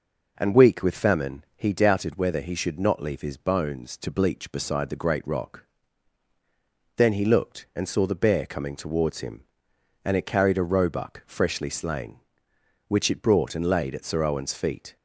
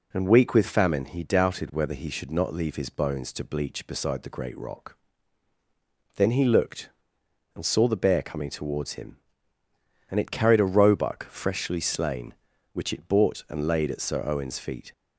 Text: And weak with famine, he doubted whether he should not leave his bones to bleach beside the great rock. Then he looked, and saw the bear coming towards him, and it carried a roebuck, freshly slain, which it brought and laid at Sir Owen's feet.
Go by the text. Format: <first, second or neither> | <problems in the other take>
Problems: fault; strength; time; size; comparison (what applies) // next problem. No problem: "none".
first | says "bought" for "brought"; at 13.0 s